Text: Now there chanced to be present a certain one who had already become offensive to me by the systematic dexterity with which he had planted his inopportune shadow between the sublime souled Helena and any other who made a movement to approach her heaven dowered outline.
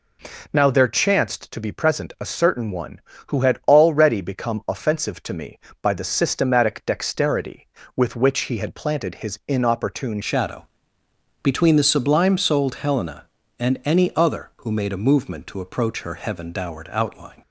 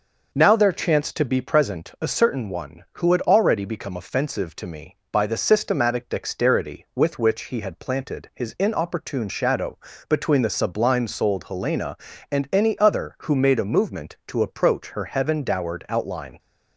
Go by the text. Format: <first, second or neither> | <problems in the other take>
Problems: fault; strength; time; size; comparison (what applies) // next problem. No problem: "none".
second | changes voice at "shadow"; from 10.2 s on; 7.2 s long // pauses between "shadow" and "between"; noticeable; at 10.6 s; 0.76 s long; slight in the second